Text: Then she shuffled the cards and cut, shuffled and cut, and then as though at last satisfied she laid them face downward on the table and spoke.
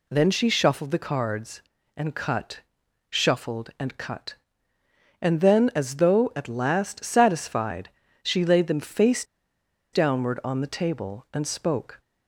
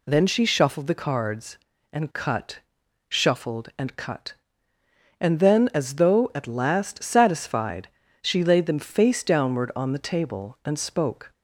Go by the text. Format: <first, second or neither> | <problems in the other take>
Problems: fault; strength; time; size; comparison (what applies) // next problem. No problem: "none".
second | pauses between "satisfied" and "she"; slight; at 7.8 s; 0.34 s long; slight in the second // pauses between "face" and "downward"; noticeable; at 9.2 s; 0.69 s long